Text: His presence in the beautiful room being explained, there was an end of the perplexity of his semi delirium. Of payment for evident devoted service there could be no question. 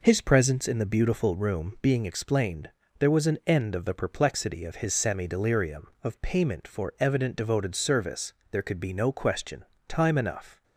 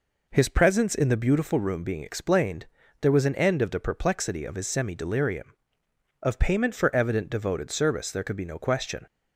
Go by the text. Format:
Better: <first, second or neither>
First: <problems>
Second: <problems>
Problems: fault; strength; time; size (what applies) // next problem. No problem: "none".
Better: second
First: pauses between "service" and "there"; slight; at 8.3 s; 0.18 s long // goes on to say "Time enough"; noticeable; from 9.8 s on; 0.76 s long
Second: none